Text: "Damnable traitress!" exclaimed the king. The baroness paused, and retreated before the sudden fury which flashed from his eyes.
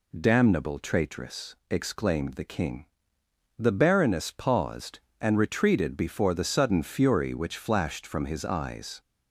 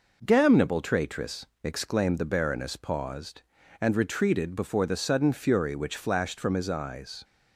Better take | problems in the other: first | skips "the king"; at 2.1 s

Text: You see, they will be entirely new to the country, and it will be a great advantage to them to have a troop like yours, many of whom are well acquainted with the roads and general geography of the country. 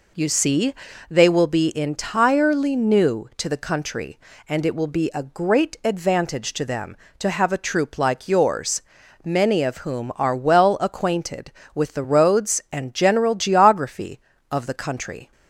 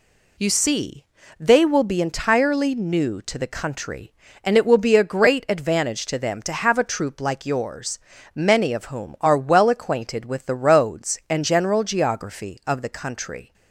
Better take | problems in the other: neither | none

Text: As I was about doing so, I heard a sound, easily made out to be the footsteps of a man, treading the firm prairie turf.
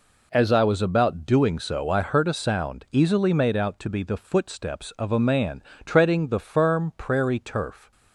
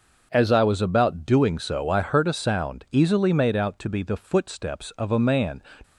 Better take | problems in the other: first | stops before "treading the firm prairie turf"; at 5.8 s

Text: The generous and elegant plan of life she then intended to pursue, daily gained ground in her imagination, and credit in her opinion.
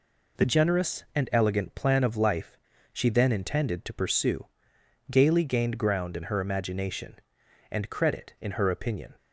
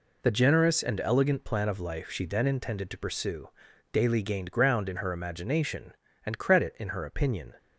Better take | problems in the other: second | pauses between "life" and "she"; slight; at 2.5 s; 0.34 s long // says "gaily" for "daily"; at 5.1 s

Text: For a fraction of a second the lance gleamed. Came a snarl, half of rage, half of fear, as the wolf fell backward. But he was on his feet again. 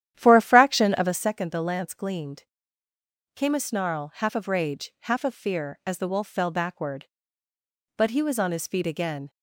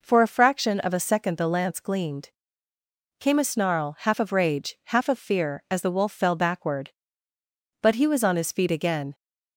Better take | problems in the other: second | starts louder than the rest; strong; until 1.2 s; 11 dB

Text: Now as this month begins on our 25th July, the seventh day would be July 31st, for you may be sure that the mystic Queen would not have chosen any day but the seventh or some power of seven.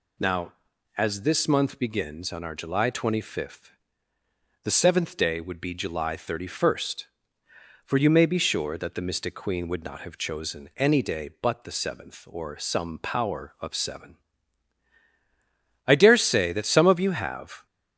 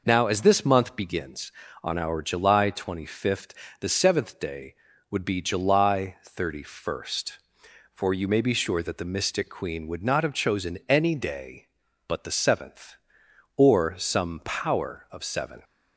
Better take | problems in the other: second | goes on to say "I dare say that some of you have"; strong; from 15.8 s on; 1.8 s long

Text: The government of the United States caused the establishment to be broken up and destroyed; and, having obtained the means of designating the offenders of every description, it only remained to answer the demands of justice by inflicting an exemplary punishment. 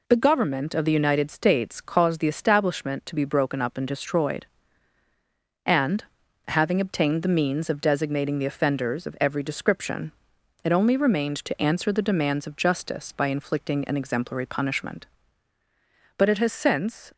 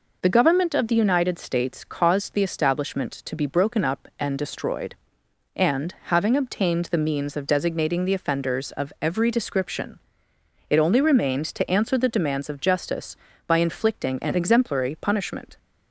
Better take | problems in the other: second | goes on to say "But it has since"; noticeable; from 16.1 s on; 0.96 s long

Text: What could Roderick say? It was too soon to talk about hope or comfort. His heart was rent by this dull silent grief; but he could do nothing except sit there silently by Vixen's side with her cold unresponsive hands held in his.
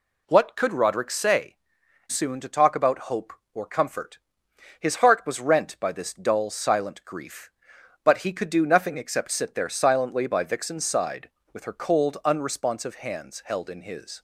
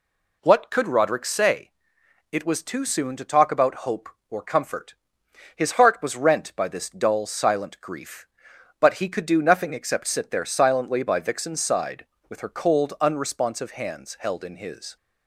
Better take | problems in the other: second | skips "It was too"; at 1.8 s

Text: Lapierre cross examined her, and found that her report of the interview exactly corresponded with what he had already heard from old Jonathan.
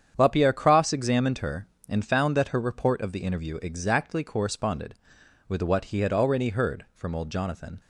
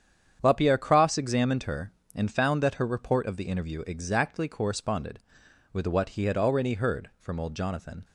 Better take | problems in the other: neither | starts louder than the rest; strong; the same in both

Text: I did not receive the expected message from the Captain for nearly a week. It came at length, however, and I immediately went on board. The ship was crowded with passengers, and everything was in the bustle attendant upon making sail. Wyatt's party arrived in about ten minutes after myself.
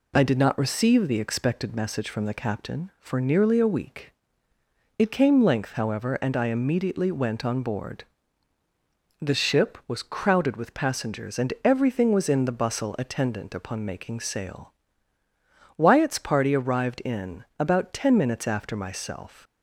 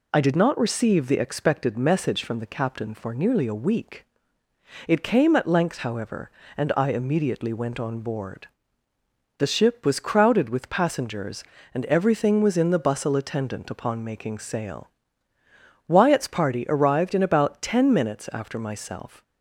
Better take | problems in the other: second | skips "at"; at 5.4 s // pauses between "in" and "about"; slight; at 17.4 s; 0.16 s long

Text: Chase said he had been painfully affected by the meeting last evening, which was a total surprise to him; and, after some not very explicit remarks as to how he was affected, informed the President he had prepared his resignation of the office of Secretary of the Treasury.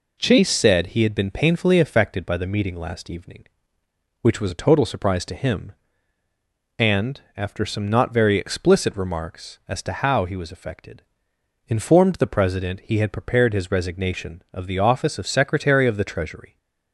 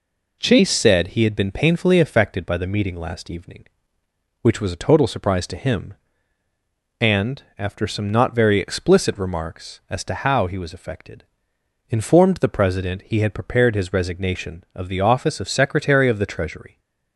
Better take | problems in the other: neither | none

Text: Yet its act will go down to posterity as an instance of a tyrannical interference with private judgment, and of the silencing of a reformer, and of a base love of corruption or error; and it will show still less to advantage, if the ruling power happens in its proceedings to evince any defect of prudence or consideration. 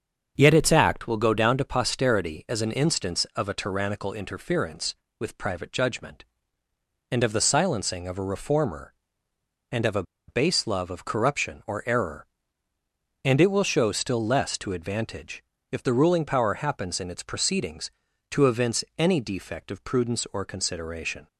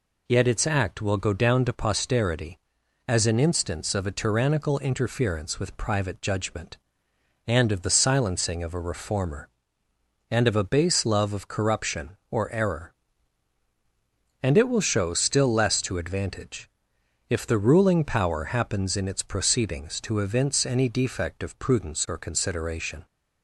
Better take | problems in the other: second | starts louder than the rest; until 1.3 s; 7 dB // pauses between "a" and "base"; slight; at 10.0 s; 0.25 s long

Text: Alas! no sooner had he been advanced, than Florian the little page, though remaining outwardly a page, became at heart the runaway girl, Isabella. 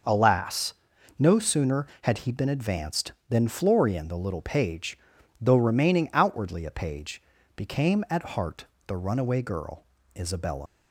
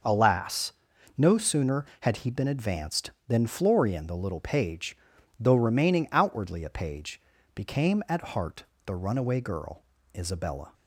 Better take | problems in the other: second | starts louder than the rest; noticeable; until 1.5 s; 6 dB; noticeable in the second // pauses between "heart" and "the"; slight; at 8.6 s; 0.20 s long; slight in the second // leaves "Isabella" unfinished; at 10.6 s; 85 ms

